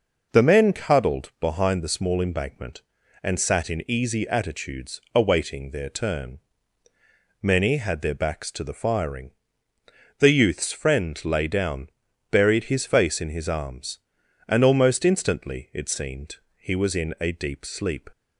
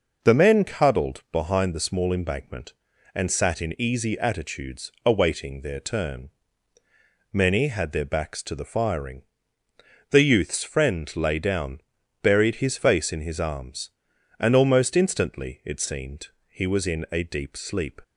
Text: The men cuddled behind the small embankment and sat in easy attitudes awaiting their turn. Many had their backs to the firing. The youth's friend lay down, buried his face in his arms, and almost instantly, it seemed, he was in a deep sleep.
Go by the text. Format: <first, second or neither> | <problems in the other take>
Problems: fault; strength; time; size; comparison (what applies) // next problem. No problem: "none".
neither | none